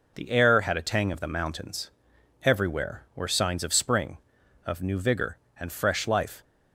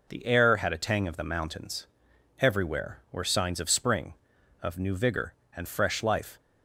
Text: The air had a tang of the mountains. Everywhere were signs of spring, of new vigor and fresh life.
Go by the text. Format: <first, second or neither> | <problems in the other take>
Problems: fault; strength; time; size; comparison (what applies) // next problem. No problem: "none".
neither | none